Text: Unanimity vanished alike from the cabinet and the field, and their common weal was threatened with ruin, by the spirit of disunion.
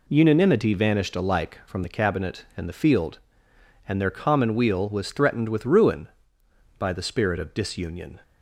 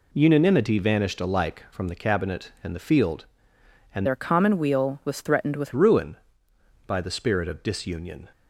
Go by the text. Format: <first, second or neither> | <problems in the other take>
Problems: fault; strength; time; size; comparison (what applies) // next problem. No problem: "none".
first | changes voice from "their" to "with"; from 4.0 to 5.7 s; 1.7 s long